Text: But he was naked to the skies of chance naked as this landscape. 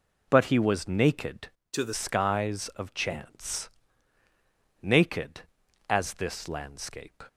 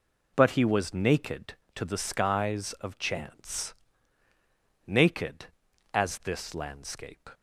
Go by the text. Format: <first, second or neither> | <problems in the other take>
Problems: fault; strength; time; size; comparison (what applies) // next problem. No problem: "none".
second | changes voice from "to" to "the"; from 1.7 to 1.9 s; 0.2 s long // pauses between "chance" and "naked"; at 3.6 s; 1.1 s long; also in the second